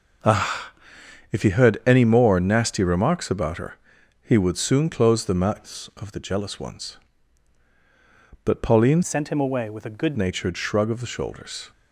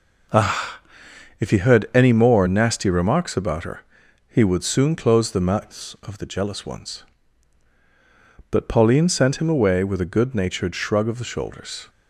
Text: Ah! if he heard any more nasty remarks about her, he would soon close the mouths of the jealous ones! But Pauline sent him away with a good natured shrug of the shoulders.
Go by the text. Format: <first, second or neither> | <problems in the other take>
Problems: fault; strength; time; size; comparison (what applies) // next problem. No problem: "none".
second | changes voice from "sent" to "good"; from 9.0 to 10.1 s; 1.1 s long